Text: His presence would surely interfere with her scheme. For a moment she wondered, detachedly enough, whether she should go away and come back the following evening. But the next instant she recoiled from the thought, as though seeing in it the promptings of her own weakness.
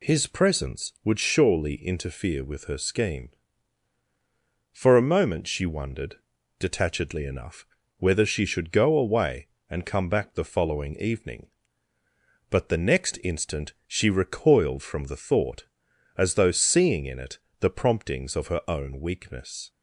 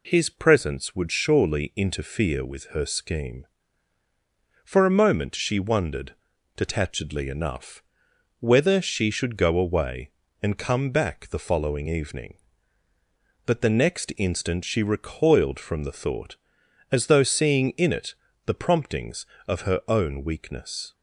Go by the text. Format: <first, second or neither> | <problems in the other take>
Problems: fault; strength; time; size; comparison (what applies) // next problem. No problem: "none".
neither | pauses between "it" and "the"; slight; the same in both